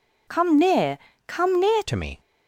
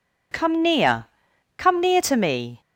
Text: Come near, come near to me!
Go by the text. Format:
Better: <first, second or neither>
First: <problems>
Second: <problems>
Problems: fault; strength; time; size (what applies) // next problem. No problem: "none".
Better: second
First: changes voice at "to"; from 1.8 s on; 0.3 s long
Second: none